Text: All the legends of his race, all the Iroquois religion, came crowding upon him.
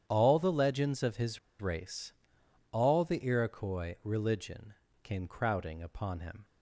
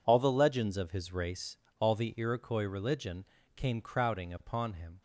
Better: second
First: starts louder than the rest; strong; until 1.0 s; 9.5 dB // pauses between "his" and "race"; slight; at 1.3 s; 0.21 s long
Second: none

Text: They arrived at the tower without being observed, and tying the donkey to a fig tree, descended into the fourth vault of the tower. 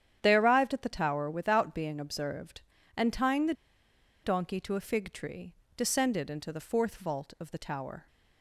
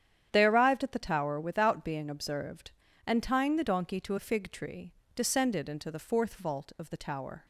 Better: second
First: starts louder than the rest; strong; until 1.2 s; 9.5 dB // pauses between "the" and "donkey"; noticeable; at 3.5 s; 0.70 s long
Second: starts louder than the rest; strong; until 1.3 s; 9.5 dB

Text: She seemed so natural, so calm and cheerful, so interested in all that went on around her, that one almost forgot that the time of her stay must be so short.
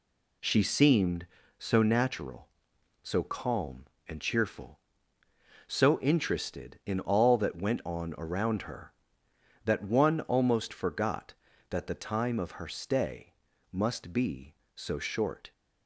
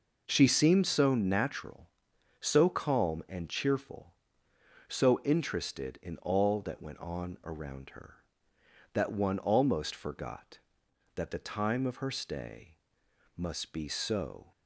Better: first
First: pauses between "stay" and "must"; at 13.3 s; 0.38 s long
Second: pauses between "stay" and "must"; noticeable; at 12.7 s; 0.60 s long // stops before "short"; at 14.5 s

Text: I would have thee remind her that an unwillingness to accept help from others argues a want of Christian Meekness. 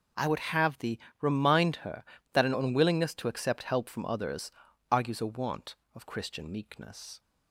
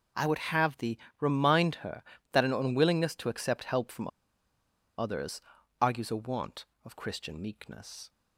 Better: first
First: pauses between "thee" and "remind"; slight; at 0.9 s; 0.22 s long // pauses between "others" and "argues"; at 4.4 s; 0.40 s long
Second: pauses between "thee" and "remind"; slight; at 0.9 s; 0.22 s long // pauses between "from" and "others"; noticeable; at 4.0 s; 0.90 s long // pauses between "others" and "argues"; at 5.3 s; 0.40 s long

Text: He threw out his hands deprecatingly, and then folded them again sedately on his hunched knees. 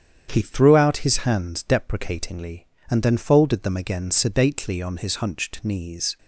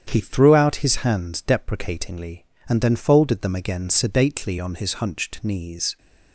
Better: neither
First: starts louder than the rest; strong; until 1.3 s; 8.5 dB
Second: starts louder than the rest; strong; until 1.0 s; 8.5 dB

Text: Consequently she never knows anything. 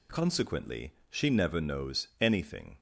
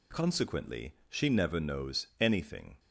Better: neither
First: pauses between "Consequently" and "she"; slight; at 0.9 s; 0.18 s long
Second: pauses between "Consequently" and "she"; slight; at 0.9 s; 0.16 s long

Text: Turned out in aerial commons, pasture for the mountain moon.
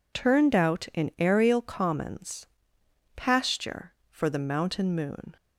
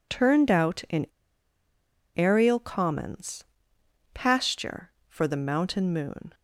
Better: first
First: none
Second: pauses between "in" and "aerial"; at 1.0 s; 1.1 s long

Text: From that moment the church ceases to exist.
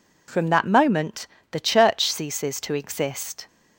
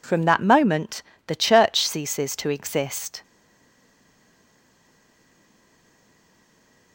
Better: first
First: pauses between "moment" and "the"; slight; at 1.2 s; 0.28 s long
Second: pauses between "moment" and "the"; slight; at 1.0 s; 0.28 s long // stays silent after the last word; strong; from 3.2 s on; 3.7 s long

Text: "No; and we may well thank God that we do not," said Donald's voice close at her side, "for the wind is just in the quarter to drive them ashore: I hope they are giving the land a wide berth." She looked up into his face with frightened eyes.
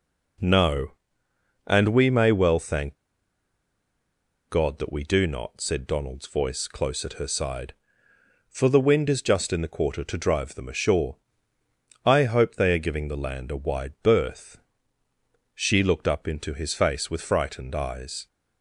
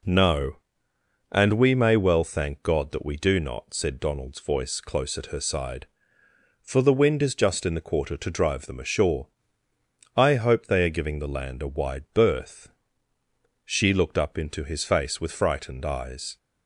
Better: second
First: pauses between "thank" and "God"; strong; at 2.9 s; 1.5 s long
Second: none

